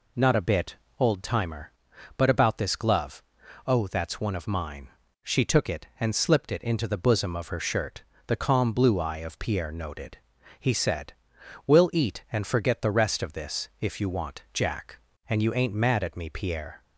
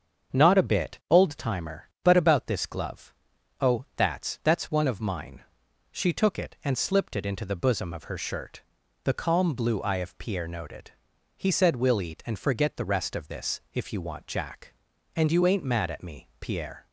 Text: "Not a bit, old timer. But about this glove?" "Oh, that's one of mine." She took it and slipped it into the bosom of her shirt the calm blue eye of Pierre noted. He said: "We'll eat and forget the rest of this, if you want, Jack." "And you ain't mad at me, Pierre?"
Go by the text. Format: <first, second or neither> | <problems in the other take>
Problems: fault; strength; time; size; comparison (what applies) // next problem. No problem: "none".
first | starts louder than the rest; strong; until 1.4 s; 7 dB // says "that's" twice; at 4.4 s // pauses between "shirt" and "the"; at 8.6 s; 0.40 s long; slight in the first